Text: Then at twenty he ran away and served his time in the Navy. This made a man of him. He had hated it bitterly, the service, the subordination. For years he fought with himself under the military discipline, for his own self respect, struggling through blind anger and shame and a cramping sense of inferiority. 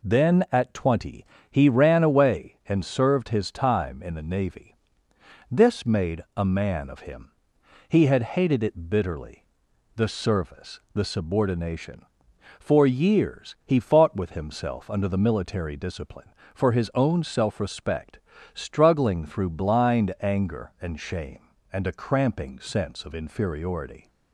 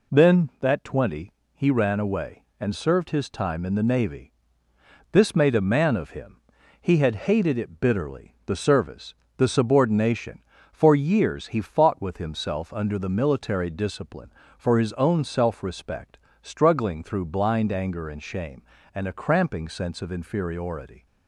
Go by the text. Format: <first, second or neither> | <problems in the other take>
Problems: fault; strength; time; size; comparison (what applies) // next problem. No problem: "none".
first | says "that" for "at"; at 0.5 s // pauses between "twenty" and "he"; slight; at 1.3 s; 0.22 s long; slight in the first